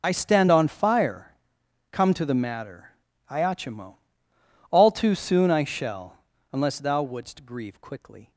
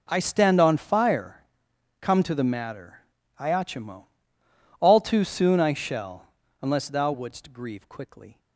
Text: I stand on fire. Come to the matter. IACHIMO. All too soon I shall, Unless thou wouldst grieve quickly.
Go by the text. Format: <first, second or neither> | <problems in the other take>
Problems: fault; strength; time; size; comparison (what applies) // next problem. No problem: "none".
second | loses the start of "I"; at 0.0 s; 35 ms